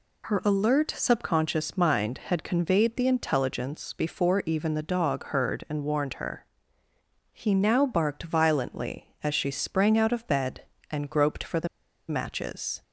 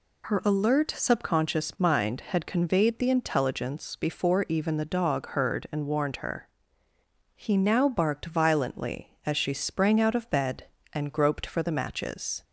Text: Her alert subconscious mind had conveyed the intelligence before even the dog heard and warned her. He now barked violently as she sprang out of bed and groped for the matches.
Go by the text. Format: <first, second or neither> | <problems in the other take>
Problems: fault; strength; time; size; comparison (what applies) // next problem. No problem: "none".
second | pauses between "the" and "matches"; at 11.6 s; 0.42 s long